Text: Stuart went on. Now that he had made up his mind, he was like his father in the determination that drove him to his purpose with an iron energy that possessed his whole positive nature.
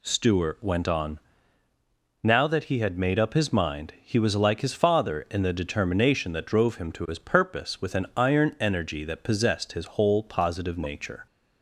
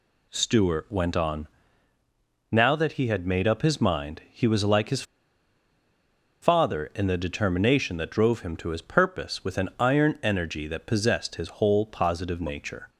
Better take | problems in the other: first | pauses between "his" and "father"; strong; at 5.0 s; 1.3 s long

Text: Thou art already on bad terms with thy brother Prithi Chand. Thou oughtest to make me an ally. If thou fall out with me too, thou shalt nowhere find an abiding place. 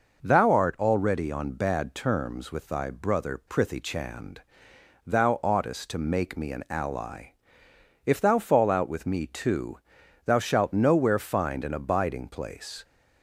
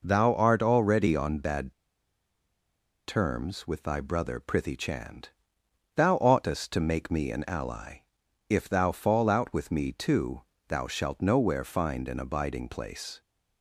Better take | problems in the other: first | pauses between "bad" and "terms"; strong; at 1.7 s; 1.3 s long

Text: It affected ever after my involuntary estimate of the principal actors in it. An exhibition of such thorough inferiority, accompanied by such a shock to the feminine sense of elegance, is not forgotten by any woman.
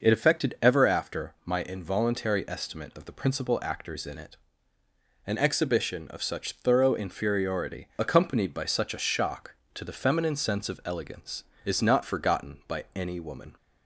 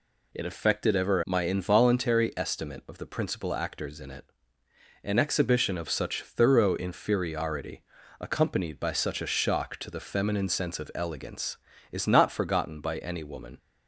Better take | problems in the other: first | skips "after"; at 1.2 s

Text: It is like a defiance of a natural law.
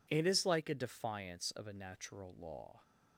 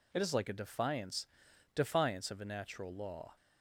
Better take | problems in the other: first | says "defiance" twice; at 1.7 s

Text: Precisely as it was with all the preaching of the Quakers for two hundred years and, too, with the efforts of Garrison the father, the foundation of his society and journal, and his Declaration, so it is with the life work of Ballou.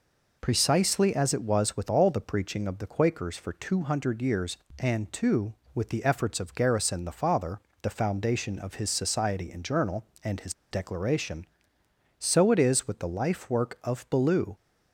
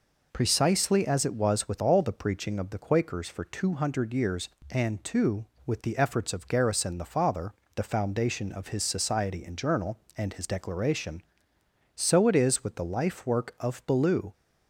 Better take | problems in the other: second | pauses between "his" and "Declaration"; slight; at 10.5 s; 0.18 s long

